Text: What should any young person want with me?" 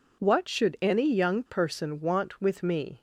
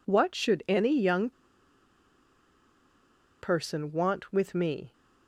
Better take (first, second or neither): first